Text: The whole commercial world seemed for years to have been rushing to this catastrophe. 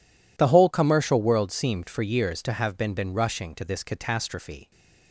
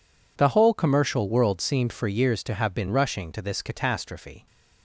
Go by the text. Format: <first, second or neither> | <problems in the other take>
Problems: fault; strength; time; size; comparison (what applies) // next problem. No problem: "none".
second | says "been" twice; at 2.9 s